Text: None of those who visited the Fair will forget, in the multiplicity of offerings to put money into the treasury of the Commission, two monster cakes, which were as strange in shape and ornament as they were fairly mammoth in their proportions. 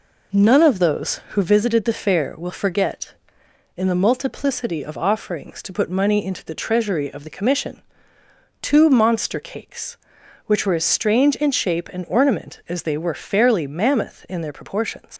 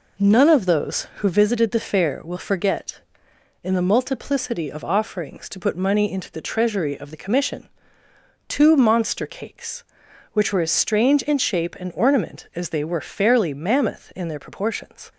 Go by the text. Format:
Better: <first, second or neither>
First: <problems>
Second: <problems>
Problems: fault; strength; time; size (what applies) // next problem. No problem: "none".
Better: second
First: leaves "proportions" unfinished; at 15.1 s; 75 ms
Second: none